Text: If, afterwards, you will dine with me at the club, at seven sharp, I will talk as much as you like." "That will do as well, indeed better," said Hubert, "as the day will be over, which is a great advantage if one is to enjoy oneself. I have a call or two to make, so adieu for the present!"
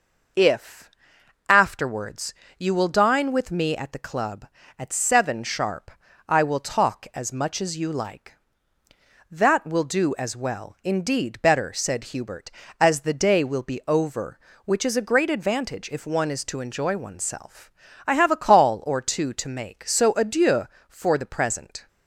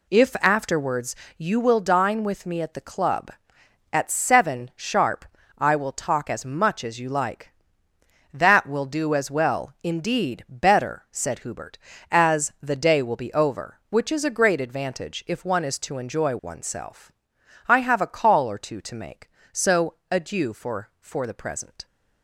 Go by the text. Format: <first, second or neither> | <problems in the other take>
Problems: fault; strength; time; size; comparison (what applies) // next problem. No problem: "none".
first | pauses between "so" and "adieu"; slight; at 19.9 s; 0.18 s long // says "for" twice; at 20.9 s